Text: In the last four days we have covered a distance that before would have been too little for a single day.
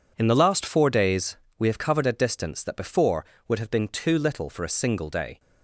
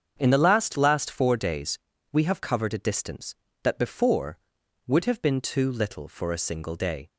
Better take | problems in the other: first | starts louder than the rest; strong; until 1.2 s; 7.5 dB // says "last" twice; at 0.7 s // pauses between "days" and "we"; slight; at 1.7 s; 0.34 s long; slight in the first

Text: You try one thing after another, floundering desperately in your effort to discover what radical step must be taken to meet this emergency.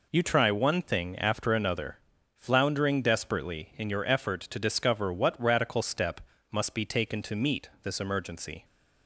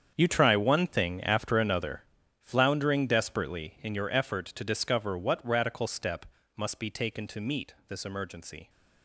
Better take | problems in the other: first | gets quieter; strong; throughout; 13.5 dB // pauses between "step" and "must"; slight; at 6.2 s; 0.28 s long; slight in the first

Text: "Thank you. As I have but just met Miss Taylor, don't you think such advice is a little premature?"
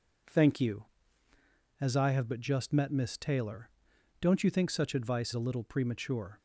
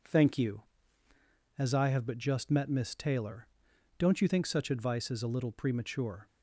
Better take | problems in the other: second | skips "is"; at 5.3 s

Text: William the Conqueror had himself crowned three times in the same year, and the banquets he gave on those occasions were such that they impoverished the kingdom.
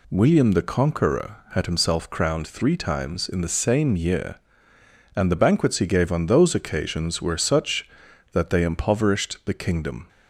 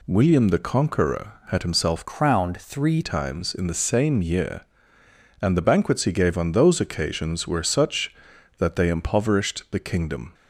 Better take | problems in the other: first | changes voice from "crowned" to "three"; from 2.0 to 3.0 s; 1.0 s long

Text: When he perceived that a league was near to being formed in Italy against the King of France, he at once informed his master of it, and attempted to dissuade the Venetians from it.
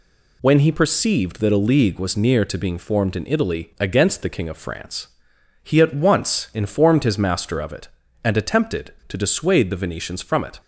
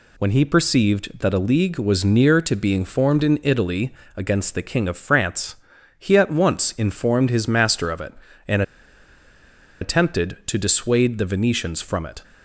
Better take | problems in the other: first | pauses between "Italy" and "against"; slight; at 3.9 s; 0.24 s long // pauses between "and" and "attempted"; at 8.6 s; 1.1 s long

